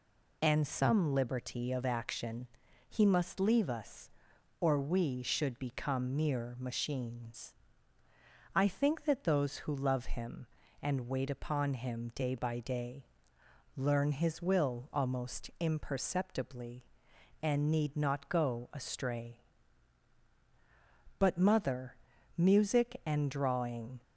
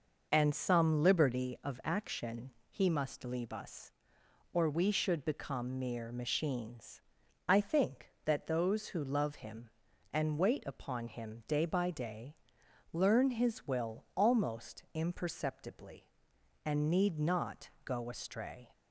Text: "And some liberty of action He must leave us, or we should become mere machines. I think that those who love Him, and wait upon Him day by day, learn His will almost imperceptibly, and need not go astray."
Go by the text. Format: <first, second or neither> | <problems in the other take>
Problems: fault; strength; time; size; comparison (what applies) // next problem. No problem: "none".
second | pauses between "action" and "He"; at 2.4 s; 0.42 s long; slight in the second // goes on to say "But mother music and drawing"; strong; from 21.1 s on; 2.8 s long